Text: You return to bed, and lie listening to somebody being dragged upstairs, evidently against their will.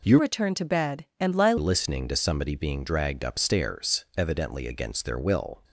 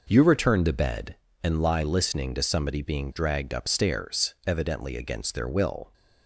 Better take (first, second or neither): second